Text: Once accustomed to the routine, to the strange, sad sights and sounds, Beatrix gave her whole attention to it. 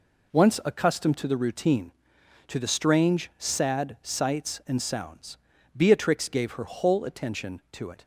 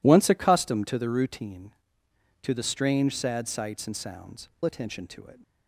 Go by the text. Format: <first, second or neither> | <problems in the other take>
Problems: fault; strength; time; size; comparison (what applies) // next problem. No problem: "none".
first | skips "Beatrix gave her whole"; at 4.5 s